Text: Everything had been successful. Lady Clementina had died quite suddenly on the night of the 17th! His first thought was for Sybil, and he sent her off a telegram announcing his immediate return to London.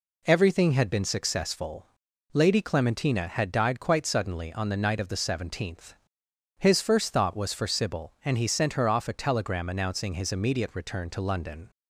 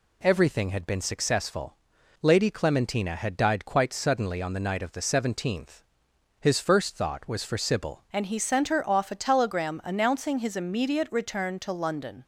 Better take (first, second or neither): first